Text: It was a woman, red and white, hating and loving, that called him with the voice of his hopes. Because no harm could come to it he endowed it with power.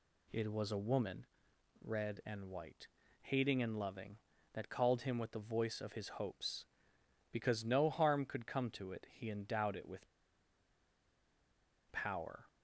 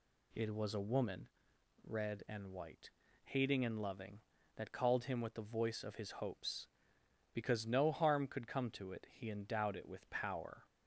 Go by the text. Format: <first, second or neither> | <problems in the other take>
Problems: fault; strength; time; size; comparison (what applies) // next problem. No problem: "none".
second | pauses between "with" and "power"; strong; at 10.0 s; 1.8 s long